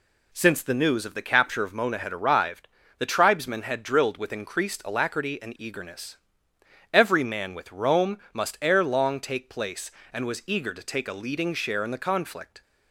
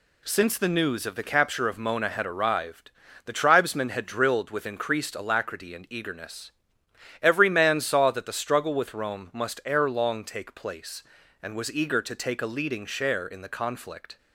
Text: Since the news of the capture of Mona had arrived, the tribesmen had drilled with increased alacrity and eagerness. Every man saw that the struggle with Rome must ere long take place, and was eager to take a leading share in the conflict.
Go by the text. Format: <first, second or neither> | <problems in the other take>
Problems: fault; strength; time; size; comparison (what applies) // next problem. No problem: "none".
second | skips "saw that the struggle"; at 7.5 s // pauses between "Rome" and "must"; slight; at 8.1 s; 0.16 s long